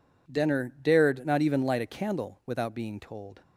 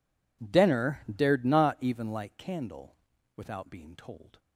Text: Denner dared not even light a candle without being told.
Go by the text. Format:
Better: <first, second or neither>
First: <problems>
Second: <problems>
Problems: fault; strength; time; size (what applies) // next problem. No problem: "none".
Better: first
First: none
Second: skips "a"; at 2.3 s // pauses between "candle" and "without"; at 2.9 s; 0.40 s long